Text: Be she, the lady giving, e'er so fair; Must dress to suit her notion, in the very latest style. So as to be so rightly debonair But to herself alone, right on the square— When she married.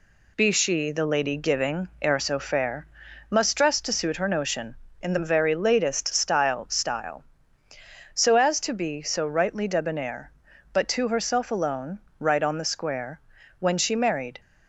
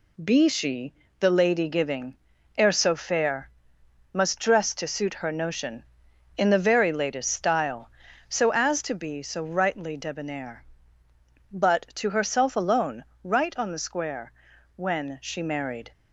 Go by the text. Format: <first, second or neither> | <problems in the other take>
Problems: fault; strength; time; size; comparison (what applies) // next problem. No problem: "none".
second | says "style" twice; at 6.6 s